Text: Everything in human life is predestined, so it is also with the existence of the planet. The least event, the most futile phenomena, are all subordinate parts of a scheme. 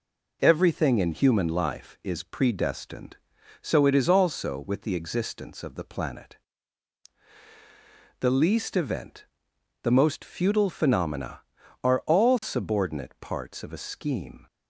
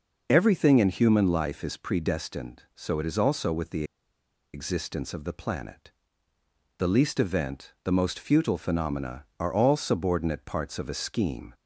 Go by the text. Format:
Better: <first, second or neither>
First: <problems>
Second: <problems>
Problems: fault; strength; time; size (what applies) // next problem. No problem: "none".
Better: first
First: none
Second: pauses between "the" and "existence"; noticeable; at 3.8 s; 0.69 s long